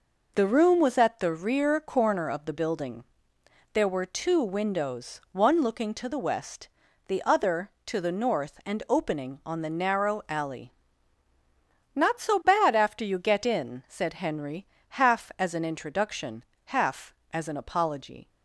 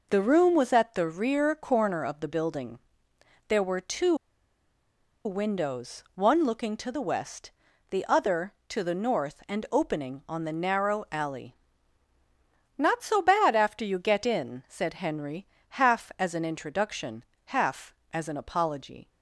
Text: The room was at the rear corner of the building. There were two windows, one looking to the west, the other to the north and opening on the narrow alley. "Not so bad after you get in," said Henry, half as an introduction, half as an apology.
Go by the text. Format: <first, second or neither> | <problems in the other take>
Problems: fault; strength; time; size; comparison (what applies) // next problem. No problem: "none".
first | pauses between "two" and "windows"; at 4.1 s; 1.0 s long